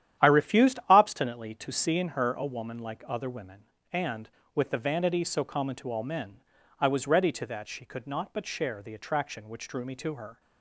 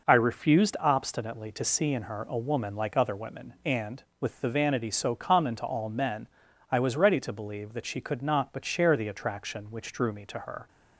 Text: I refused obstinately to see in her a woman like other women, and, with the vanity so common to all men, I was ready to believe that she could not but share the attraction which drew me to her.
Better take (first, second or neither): second